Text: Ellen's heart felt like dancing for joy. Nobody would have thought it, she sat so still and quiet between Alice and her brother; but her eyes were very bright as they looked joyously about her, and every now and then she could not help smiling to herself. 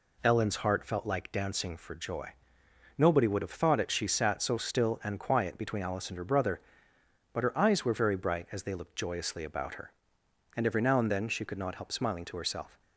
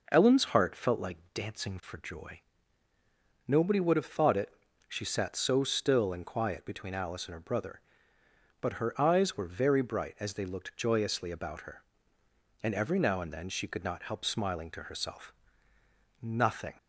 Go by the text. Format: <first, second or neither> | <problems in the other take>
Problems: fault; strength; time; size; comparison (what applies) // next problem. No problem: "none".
first | pauses between "like" and "dancing"; slight; at 1.1 s; 0.18 s long // goes on to say "Nothing"; from 16.2 s on; 0.50 s long